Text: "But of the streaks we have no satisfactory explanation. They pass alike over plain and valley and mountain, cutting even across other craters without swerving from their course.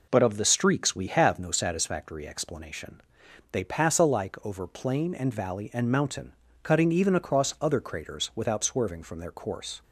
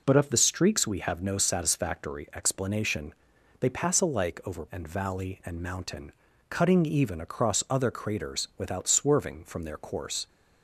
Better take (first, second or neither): first